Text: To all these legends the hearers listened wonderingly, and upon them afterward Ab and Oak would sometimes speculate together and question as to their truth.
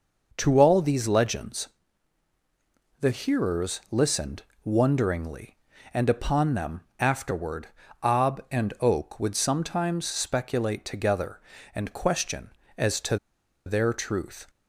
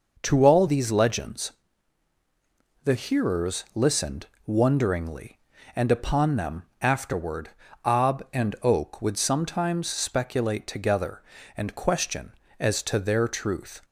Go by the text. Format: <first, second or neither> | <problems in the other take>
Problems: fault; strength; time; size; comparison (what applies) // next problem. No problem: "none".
second | pauses between "legends" and "the"; strong; at 1.6 s; 1.3 s long; strong in the second // pauses between "listened" and "wonderingly"; slight; at 4.4 s; 0.20 s long; slight in the second // pauses between "them" and "afterward"; slight; at 6.8 s; 0.18 s long; slight in the second // pauses between "afterward" and "Ab"; slight; at 7.6 s; 0.36 s long; slight in the second // pauses between "to" and "their"; noticeable; at 13.1 s; 0.49 s long